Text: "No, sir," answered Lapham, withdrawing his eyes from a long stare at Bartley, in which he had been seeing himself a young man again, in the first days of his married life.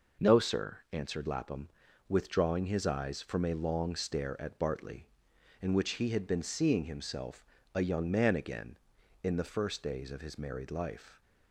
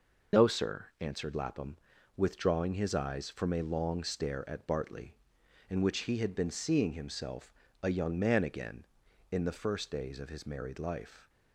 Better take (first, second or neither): first